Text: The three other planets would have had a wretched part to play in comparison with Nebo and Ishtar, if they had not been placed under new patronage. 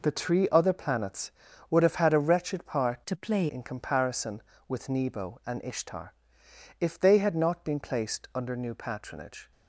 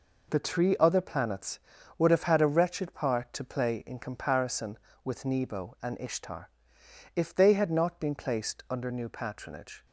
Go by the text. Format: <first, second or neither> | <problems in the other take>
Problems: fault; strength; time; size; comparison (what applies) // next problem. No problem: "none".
second | changes voice from "to" to "play"; from 3.0 to 3.4 s; 0.4 s long